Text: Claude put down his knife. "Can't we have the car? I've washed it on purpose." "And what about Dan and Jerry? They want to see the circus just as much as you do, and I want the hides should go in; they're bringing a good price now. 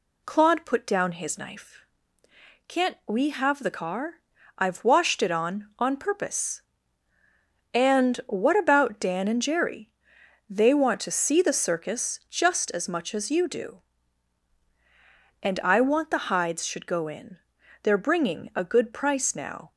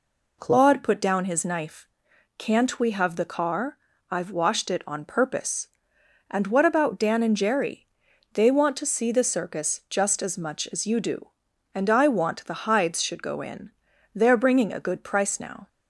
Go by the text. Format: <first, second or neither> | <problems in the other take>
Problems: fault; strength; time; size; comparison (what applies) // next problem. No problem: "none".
second | says "on" twice; at 5.7 s